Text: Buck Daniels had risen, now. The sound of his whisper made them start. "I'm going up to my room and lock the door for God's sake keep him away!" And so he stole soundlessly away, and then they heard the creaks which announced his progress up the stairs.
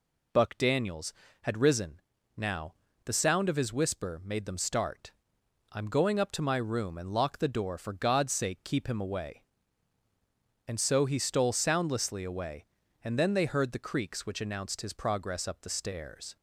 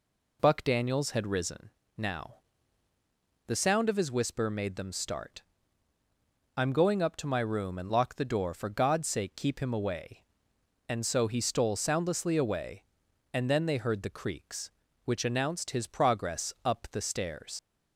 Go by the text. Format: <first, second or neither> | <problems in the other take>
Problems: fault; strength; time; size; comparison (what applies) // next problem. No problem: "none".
first | leaves "stairs" unfinished; at 17.5 s; 75 ms